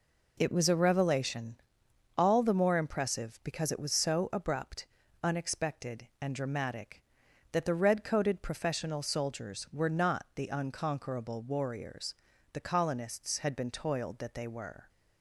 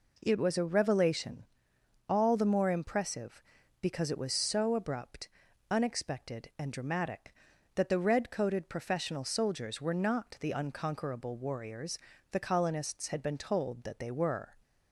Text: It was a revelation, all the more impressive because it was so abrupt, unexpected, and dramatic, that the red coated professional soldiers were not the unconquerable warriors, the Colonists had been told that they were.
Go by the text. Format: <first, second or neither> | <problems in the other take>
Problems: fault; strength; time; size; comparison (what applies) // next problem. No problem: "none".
second | says "toiled" for "told"; at 13.7 s